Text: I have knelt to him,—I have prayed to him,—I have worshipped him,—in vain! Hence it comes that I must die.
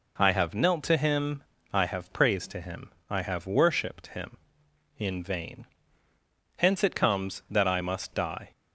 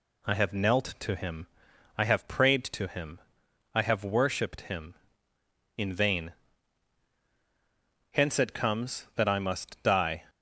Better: second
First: says "praised" for "prayed"; at 2.1 s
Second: none

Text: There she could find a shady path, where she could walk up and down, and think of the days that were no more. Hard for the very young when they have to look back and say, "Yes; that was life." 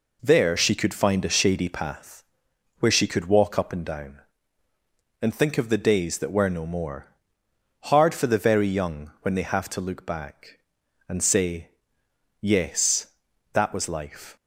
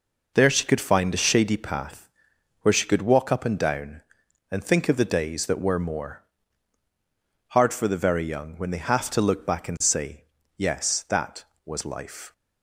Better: first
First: none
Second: skips "no"; at 5.7 s

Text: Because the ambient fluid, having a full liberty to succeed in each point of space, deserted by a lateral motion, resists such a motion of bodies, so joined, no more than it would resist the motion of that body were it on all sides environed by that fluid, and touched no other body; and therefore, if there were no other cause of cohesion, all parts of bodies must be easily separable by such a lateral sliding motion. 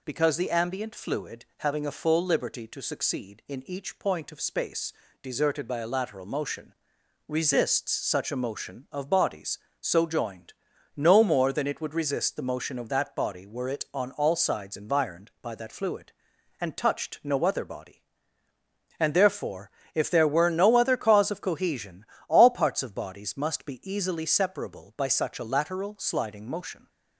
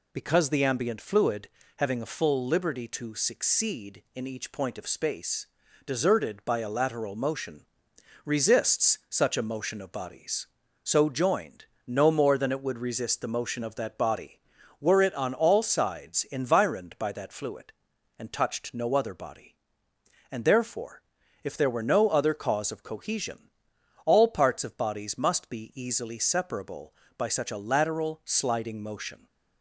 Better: neither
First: none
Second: none

